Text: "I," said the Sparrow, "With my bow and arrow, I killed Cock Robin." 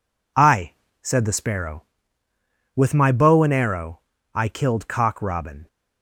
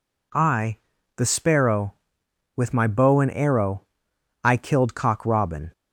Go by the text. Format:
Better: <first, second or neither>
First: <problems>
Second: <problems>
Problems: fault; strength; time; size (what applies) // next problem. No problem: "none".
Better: first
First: none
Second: skips "said"; at 0.9 s